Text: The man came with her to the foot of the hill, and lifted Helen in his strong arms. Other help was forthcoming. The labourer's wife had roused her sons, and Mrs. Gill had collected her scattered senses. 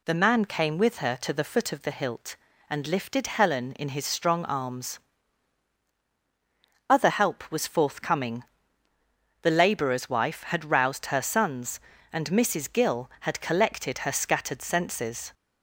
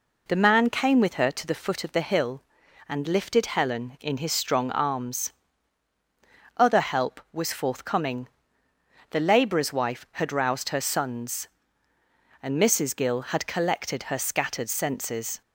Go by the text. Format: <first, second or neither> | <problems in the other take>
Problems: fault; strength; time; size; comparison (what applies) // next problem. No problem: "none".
second | says "hilt" for "hill"; at 1.9 s